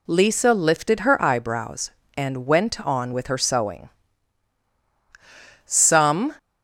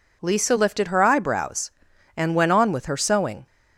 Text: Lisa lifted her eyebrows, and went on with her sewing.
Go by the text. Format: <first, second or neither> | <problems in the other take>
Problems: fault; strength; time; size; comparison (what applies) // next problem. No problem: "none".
second | goes on to say "Some"; noticeable; from 5.6 s on; 0.70 s long